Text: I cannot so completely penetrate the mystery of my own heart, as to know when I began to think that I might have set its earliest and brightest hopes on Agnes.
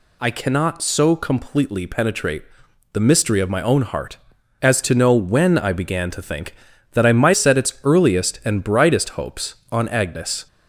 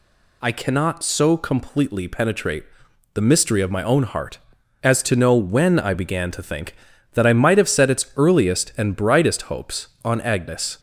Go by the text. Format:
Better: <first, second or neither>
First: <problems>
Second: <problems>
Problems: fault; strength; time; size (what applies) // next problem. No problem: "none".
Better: second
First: pauses between "penetrate" and "the"; noticeable; at 2.4 s; 0.50 s long // skips "have"; at 7.3 s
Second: pauses between "penetrate" and "the"; noticeable; at 2.6 s; 0.50 s long